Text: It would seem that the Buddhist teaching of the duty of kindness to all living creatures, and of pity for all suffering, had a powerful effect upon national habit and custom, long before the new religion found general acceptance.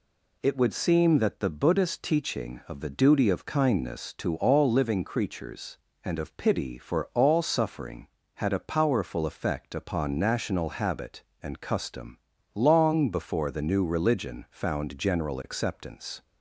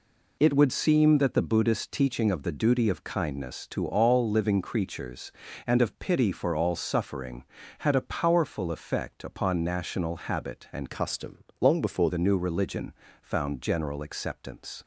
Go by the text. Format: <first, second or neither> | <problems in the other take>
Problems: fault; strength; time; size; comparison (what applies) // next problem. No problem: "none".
first | changes voice from "custom" to "before"; from 10.9 to 12.0 s; 1.1 s long // pauses between "religion" and "found"; slight; at 12.9 s; 0.28 s long